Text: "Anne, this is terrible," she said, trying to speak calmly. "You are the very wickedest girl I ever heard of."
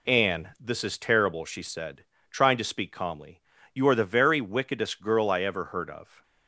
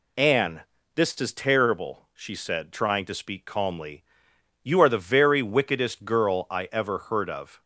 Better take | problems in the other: neither | none

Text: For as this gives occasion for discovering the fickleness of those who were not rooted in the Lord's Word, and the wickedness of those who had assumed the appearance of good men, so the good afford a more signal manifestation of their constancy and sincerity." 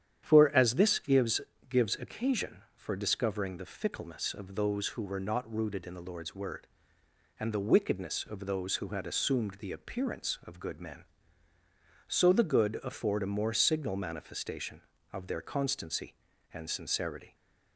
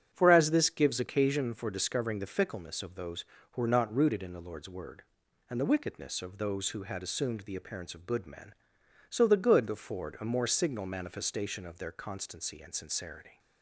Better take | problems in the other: second | starts louder than the rest; strong; until 1.2 s; 9.5 dB; strong in the second // says "gives" twice; at 1.6 s

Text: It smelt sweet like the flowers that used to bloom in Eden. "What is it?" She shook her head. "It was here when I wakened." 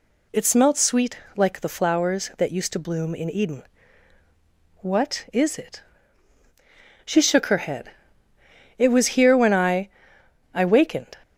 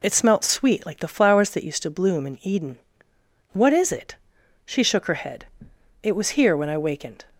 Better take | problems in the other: second | pauses between "sweet" and "like"; slight; at 1.1 s; 0.20 s long // says "I" twice; at 10.5 s

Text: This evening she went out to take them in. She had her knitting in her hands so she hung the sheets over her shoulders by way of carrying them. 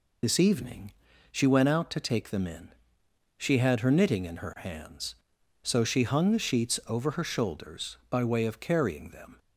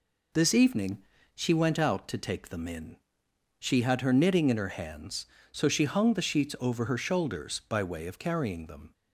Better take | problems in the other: second | loses the start of "This"; at 0.2 s; 50 ms // pauses between "evening" and "she"; at 0.9 s; 0.38 s long; slight in the second

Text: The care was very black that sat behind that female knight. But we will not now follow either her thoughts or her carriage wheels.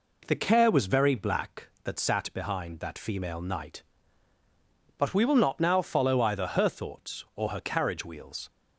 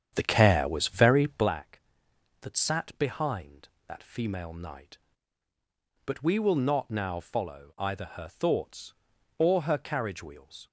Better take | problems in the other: first | starts louder than the rest; strong; until 1.5 s; 8.5 dB

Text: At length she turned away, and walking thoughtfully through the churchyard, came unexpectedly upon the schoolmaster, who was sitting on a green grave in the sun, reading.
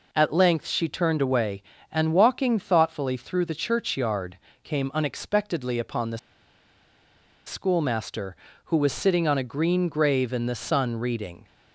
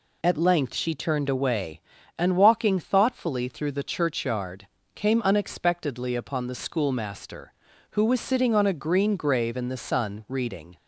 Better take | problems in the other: second | pauses between "the" and "schoolmaster"; strong; at 6.1 s; 1.2 s long

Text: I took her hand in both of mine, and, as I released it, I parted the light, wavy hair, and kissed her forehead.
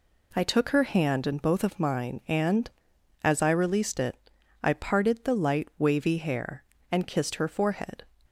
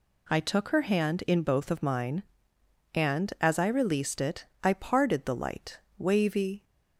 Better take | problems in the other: first | stops before "hair and kissed her forehead"; at 6.6 s

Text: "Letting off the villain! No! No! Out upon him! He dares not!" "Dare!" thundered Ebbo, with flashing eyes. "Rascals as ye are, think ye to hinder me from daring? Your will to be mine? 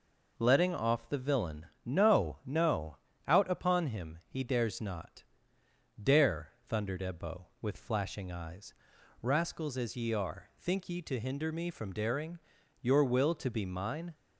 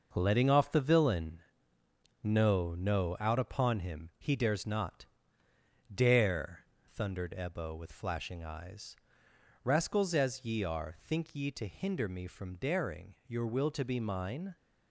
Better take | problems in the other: first | gets quieter; strong; throughout; 7.5 dB

